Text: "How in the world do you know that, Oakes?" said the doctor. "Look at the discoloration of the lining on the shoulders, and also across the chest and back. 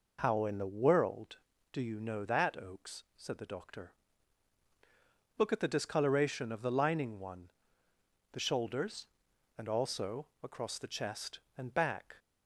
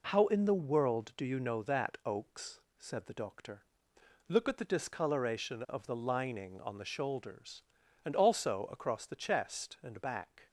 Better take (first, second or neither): second